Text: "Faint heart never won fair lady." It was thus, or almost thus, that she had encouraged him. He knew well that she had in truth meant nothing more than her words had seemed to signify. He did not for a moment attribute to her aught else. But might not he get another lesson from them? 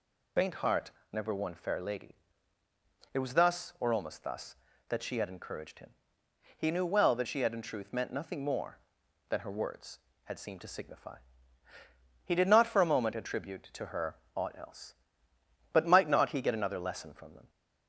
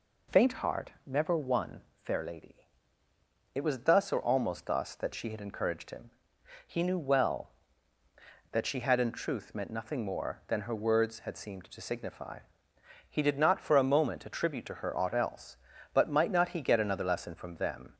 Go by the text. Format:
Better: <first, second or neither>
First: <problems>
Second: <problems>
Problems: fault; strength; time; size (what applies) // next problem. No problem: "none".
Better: second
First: loses the start of "Faint"; at 0.3 s; 45 ms // pauses between "heart" and "never"; slight; at 0.9 s; 0.20 s long // pauses between "her" and "aught"; slight; at 14.1 s; 0.18 s long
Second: pauses between "heart" and "never"; slight; at 0.9 s; 0.16 s long